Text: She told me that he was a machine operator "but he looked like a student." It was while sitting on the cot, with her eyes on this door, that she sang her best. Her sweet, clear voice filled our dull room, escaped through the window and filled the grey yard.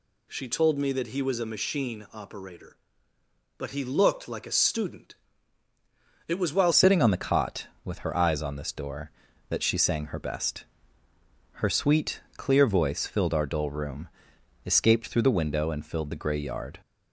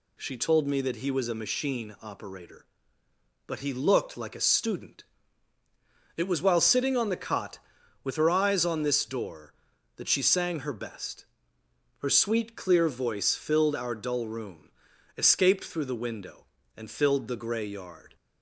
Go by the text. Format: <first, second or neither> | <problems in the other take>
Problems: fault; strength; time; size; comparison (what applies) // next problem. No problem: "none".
second | changes voice at "sitting"; from 6.7 s on; 10.0 s long